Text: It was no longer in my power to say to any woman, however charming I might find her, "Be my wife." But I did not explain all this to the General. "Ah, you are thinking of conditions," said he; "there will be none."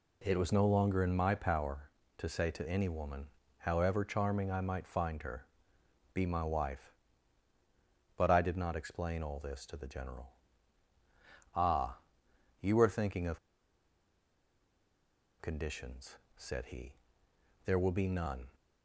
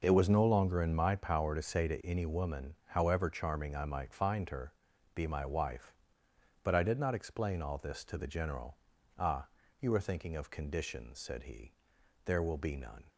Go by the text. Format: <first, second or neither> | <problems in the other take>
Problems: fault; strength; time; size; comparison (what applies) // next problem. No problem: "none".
second | pauses between "of" and "conditions"; strong; at 13.3 s; 2.0 s long